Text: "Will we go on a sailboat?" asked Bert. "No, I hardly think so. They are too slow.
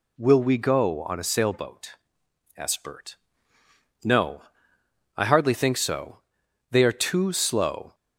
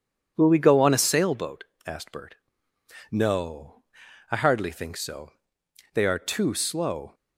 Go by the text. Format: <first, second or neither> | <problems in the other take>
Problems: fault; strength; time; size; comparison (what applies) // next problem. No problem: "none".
neither | none